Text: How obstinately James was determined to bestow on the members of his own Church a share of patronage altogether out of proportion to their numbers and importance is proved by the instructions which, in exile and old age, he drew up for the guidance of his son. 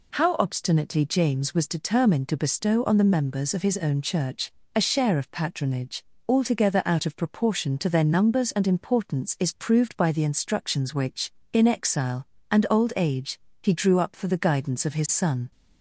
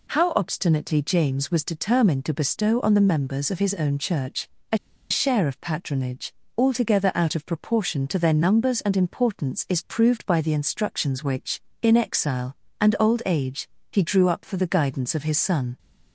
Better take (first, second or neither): first